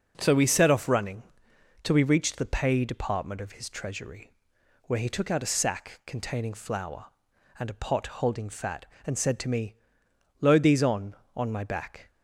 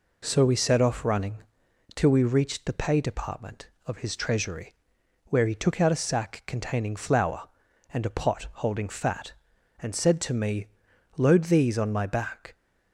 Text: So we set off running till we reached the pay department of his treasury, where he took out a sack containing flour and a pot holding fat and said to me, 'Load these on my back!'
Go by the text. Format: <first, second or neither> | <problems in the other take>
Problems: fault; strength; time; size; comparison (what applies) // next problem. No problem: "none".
second | pauses between "running" and "till"; noticeable; at 1.2 s; 0.60 s long; noticeable in the second // says "on" twice; at 11.3 s